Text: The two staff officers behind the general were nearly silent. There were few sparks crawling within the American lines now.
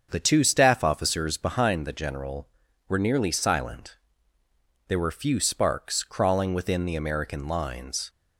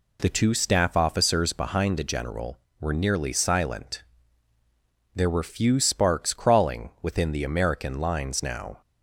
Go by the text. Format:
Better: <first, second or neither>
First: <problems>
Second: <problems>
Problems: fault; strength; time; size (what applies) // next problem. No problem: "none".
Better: second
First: starts louder than the rest; until 1.1 s; 7 dB // stops before "now"; at 8.0 s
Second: none